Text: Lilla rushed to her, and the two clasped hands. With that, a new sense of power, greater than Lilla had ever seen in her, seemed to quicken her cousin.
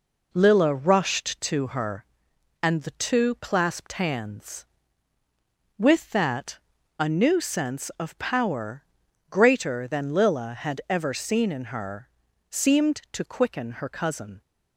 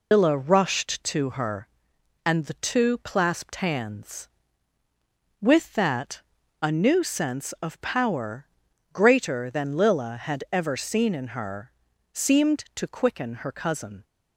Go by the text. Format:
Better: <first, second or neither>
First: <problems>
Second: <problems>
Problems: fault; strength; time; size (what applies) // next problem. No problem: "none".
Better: first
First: none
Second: loses the start of "Lilla"; at 0.1 s; 150 ms